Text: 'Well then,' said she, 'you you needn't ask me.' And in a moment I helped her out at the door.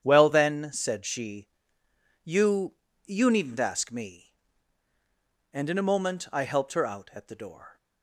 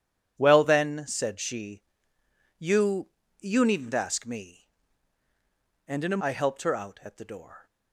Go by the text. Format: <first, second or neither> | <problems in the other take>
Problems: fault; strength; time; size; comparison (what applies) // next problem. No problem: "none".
first | starts louder than the rest; strong; until 1.3 s; 10 dB; strong in the first // pauses between "you" and "you"; slight; at 3.0 s; 0.30 s long; slight in the first // skips "moment"; at 6.2 s